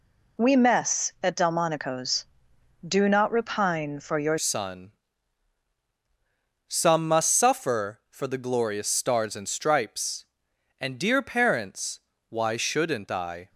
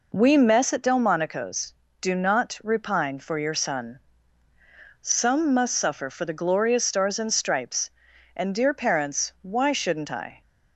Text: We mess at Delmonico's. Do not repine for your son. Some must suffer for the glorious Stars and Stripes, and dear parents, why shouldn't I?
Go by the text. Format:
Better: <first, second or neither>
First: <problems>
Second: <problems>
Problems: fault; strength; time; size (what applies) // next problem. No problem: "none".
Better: second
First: changes voice at "son"; from 4.3 s on; 9.1 s long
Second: none